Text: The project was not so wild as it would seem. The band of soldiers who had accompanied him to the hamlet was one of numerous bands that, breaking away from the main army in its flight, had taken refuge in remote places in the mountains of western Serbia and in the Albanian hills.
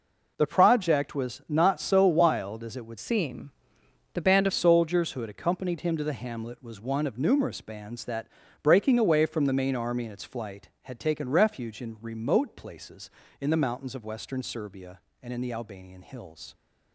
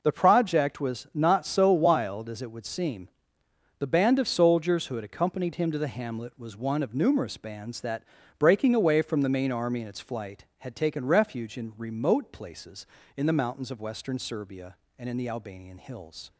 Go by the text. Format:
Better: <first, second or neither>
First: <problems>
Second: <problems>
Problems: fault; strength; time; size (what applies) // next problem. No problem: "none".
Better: second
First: changes voice from "seem" to "band"; from 2.9 to 4.4 s; 1.5 s long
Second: none